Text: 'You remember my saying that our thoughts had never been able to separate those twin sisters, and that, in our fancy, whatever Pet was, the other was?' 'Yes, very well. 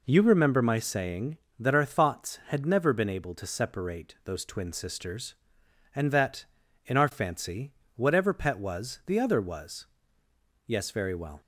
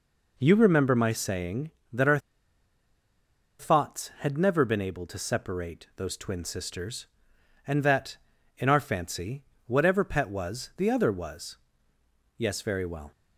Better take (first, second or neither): first